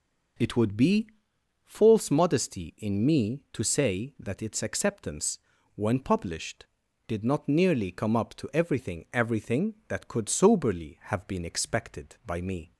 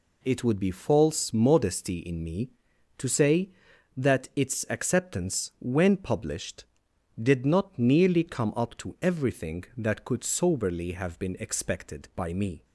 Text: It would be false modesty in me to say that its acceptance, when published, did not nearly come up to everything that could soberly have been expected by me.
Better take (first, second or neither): second